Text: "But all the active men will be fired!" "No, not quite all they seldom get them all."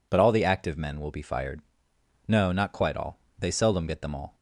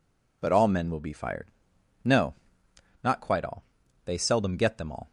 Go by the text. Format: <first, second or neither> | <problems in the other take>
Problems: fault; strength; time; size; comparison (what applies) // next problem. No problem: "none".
first | skips "the active"; at 0.6 s // pauses between "all" and "they"; at 3.6 s; 0.40 s long; slight in the first